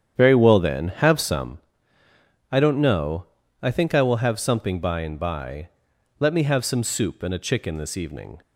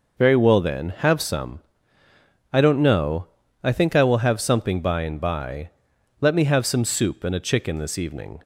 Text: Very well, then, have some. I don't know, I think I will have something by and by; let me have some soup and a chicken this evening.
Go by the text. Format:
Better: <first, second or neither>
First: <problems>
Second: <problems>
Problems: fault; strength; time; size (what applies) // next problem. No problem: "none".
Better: second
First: starts louder than the rest; strong; until 1.6 s; 9 dB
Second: none